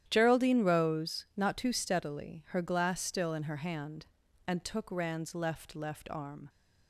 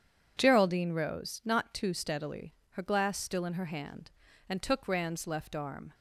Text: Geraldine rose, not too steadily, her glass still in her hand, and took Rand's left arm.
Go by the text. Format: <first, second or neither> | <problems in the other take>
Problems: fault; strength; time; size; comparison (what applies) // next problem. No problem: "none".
second | starts louder than the rest; strong; until 1.0 s; 11 dB; strong in the second // says "left" twice; at 5.7 s